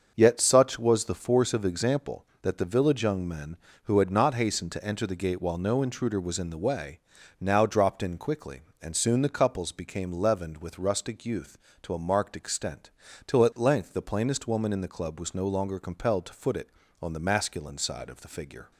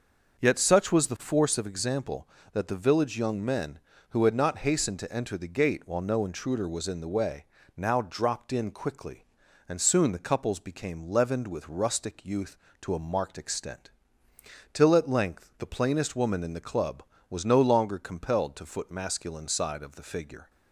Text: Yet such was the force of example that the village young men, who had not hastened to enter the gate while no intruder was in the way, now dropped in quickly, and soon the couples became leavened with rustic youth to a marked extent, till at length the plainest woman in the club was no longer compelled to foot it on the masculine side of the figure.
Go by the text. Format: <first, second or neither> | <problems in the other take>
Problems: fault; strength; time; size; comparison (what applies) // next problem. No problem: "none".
first | starts louder than the rest; until 1.4 s; 6 dB; also in the first // skips "it on the"; at 18.8 s